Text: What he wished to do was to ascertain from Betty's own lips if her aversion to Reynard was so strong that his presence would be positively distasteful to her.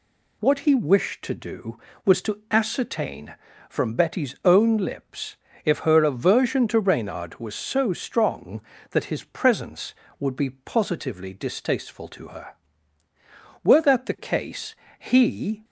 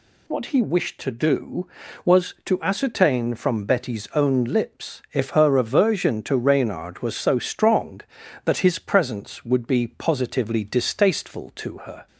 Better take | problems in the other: second | pauses between "lips" and "if"; slight; at 5.3 s; 0.30 s long // goes on to say "Were that the case he"; strong; from 13.6 s on; 2.0 s long

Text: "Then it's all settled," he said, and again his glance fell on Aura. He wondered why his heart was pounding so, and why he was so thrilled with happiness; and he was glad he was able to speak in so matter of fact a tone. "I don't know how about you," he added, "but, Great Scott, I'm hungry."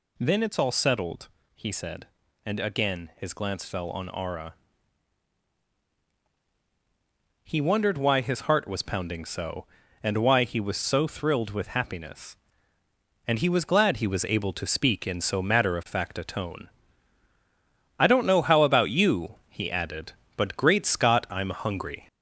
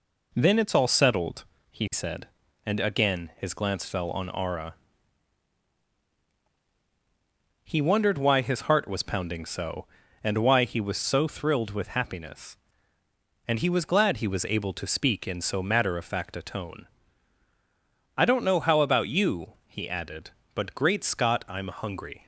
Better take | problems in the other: second | gets louder; slight; throughout; 3.5 dB

